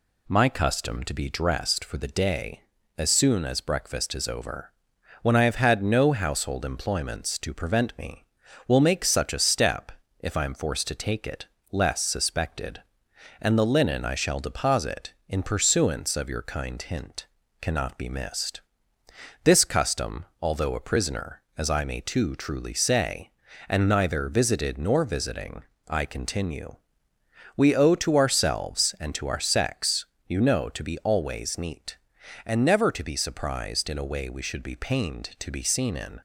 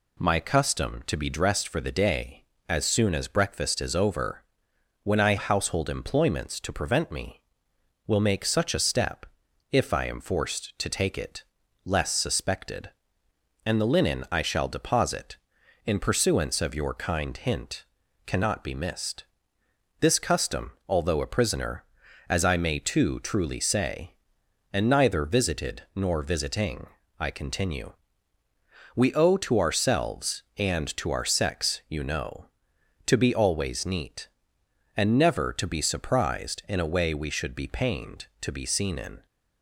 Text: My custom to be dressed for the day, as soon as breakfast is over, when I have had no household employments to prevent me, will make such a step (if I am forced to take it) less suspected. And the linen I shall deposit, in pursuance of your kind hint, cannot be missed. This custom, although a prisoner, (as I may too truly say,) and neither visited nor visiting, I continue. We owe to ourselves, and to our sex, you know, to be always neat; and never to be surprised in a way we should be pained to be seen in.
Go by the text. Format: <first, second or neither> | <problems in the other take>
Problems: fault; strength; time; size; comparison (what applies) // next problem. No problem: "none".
first | skips "have had no"; at 5.3 s